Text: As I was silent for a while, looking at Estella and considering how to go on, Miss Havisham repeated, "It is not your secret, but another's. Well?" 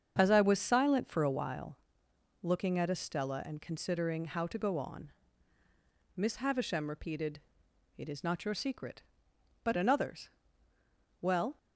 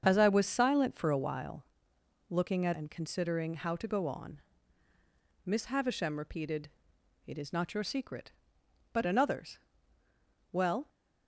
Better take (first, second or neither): first